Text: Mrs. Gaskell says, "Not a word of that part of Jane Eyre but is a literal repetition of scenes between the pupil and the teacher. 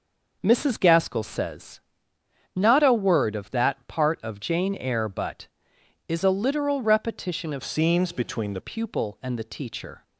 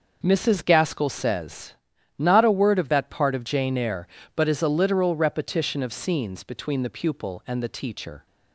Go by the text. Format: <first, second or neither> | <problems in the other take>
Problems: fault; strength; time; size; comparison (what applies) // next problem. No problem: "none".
second | changes voice from "scenes" to "the"; from 7.6 to 8.5 s; 0.9 s long